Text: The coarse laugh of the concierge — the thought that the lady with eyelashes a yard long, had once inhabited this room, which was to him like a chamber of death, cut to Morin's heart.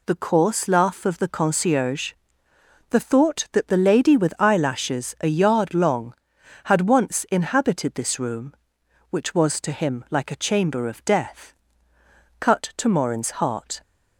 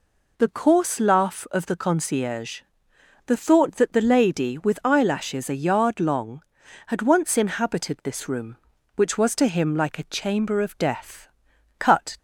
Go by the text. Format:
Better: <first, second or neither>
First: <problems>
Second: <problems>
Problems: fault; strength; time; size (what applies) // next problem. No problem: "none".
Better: first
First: none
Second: stops before "to Morin's heart"; at 12.1 s